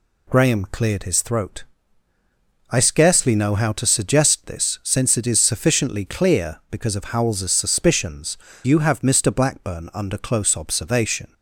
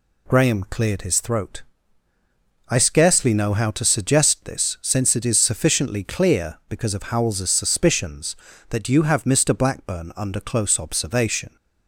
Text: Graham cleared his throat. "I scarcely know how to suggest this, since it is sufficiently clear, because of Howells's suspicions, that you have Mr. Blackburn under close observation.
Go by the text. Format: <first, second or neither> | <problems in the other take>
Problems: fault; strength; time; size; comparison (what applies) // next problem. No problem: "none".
second | skips "that"; at 8.5 s